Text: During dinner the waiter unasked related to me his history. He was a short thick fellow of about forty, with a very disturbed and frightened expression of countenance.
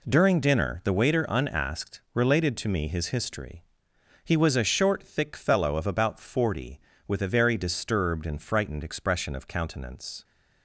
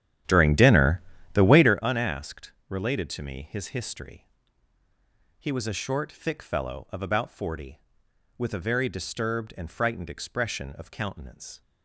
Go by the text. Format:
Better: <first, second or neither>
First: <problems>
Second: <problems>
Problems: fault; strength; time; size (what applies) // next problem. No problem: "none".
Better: first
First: none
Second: starts louder than the rest; strong; until 1.8 s; 11 dB // pauses between "dinner" and "the"; slight; at 1.0 s; 0.34 s long // pauses between "unasked" and "related"; slight; at 2.5 s; 0.16 s long